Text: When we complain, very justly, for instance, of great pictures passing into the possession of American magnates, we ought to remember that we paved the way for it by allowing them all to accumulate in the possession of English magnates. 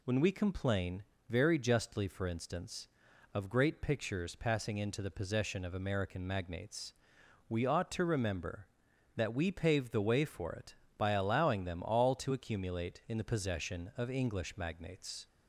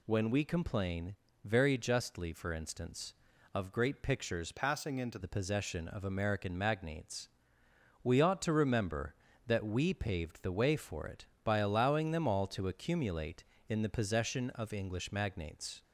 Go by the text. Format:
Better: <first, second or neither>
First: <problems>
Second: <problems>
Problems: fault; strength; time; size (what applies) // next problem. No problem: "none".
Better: first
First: none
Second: changes voice from "passing" to "into"; from 4.5 to 5.1 s; 0.6 s long